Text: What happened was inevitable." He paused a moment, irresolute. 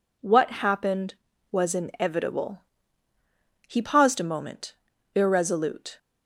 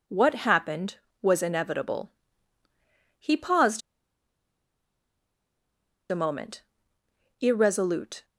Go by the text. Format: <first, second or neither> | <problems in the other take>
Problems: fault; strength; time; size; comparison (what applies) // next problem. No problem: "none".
first | pauses between "paused" and "a"; strong; at 3.8 s; 2.3 s long